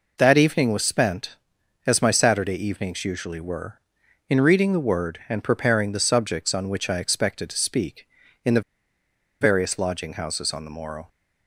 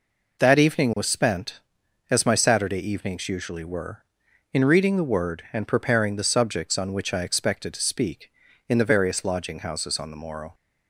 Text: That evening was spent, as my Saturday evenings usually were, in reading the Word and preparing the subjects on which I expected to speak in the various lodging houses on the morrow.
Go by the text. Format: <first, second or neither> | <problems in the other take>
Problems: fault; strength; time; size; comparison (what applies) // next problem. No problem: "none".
second | pauses between "the" and "various"; noticeable; at 8.5 s; 0.81 s long